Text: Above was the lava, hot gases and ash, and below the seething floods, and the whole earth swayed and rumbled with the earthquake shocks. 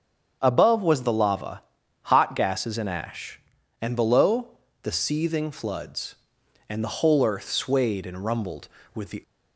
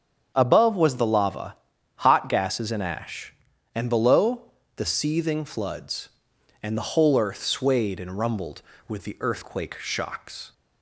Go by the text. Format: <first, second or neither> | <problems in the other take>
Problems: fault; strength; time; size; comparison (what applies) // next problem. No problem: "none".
second | starts louder than the rest; until 1.4 s; 7 dB; strong in the second // pauses between "below" and "the"; slight; at 4.4 s; 0.34 s long; slight in the second // stops before "earthquake shocks"; at 9.2 s